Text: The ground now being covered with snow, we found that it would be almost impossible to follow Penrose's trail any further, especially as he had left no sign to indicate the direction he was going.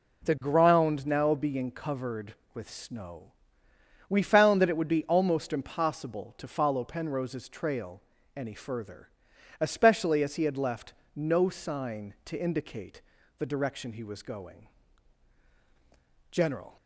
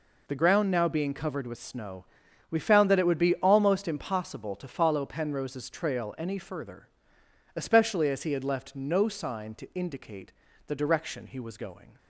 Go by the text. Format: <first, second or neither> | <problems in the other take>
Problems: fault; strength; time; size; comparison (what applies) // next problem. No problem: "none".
second | pauses between "trail" and "any"; slight; at 8.0 s; 0.34 s long // pauses between "left" and "no"; slight; at 10.9 s; 0.20 s long // pauses between "indicate" and "the"; slight; at 13.0 s; 0.36 s long; slight in the second // goes on to say "General"; slight; from 16.3 s on; 0.44 s long